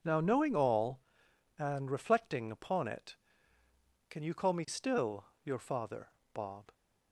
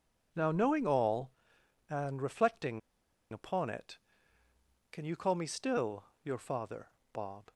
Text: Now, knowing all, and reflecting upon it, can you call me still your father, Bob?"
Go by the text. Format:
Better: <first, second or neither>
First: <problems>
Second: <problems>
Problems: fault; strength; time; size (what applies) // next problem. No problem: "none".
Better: first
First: pauses between "still" and "your"; slight; at 5.2 s; 0.20 s long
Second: pauses between "reflecting" and "upon"; noticeable; at 2.7 s; 0.51 s long // pauses between "still" and "your"; slight; at 6.0 s; 0.20 s long